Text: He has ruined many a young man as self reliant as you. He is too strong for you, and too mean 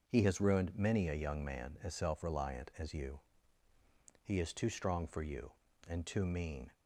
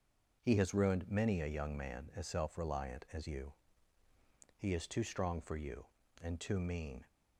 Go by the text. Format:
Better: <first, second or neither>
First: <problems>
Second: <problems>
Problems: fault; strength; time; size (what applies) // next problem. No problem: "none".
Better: neither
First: starts louder than the rest; noticeable; until 1.0 s; 6 dB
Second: starts louder than the rest; noticeable; until 1.4 s; 6 dB